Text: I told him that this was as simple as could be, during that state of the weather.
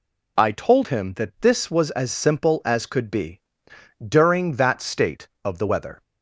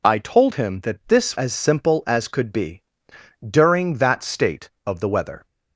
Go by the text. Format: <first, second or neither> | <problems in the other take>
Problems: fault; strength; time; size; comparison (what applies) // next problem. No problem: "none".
first | skips "was"; at 1.3 s